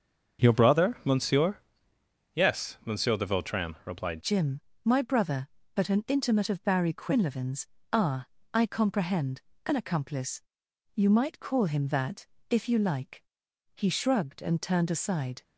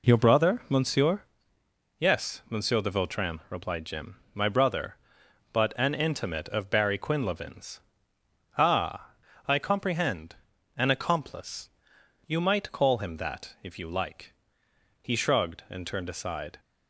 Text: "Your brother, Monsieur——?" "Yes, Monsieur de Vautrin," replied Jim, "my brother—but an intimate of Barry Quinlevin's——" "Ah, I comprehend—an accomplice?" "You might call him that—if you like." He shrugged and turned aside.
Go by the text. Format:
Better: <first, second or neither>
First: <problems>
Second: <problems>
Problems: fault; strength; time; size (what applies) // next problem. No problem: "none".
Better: second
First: starts louder than the rest; until 1.5 s; 6.5 dB // changes voice at "Jim"; from 4.2 s on; 11.2 s long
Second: none